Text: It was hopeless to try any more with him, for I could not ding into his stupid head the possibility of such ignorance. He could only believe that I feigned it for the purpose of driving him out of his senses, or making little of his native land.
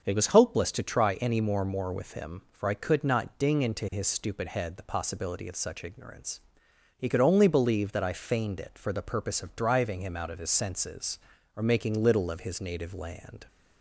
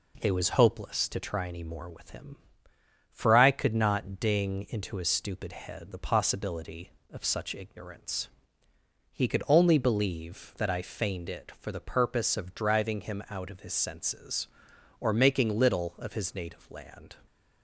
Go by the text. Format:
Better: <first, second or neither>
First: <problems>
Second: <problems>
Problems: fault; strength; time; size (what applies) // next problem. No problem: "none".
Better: second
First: starts louder than the rest; until 1.0 s; 7 dB // says "more" twice; at 1.6 s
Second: none